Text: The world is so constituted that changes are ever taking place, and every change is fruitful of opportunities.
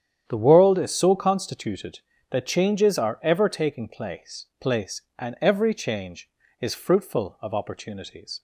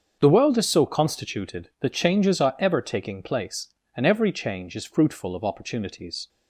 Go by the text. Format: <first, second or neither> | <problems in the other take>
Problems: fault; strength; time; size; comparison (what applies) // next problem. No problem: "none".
second | starts louder than the rest; strong; until 1.2 s; 9 dB; also in the second // says "place" twice; at 4.5 s